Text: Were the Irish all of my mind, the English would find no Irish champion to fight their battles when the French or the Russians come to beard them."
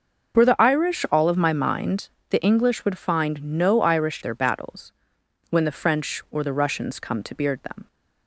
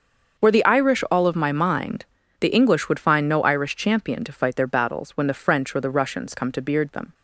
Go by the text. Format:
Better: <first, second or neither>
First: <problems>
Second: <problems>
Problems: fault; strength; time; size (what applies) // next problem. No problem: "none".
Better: second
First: starts louder than the rest; noticeable; until 1.4 s; 6 dB // skips "champion to fight"; at 4.2 s // pauses between "battles" and "when"; noticeable; at 4.9 s; 0.56 s long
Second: starts louder than the rest; until 1.4 s; 6.5 dB